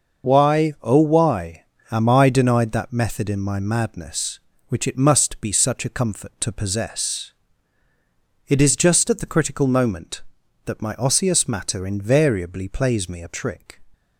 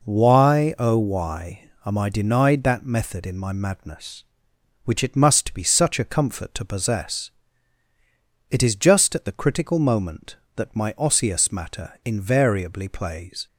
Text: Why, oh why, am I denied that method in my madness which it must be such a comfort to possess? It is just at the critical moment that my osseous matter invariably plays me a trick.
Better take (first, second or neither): first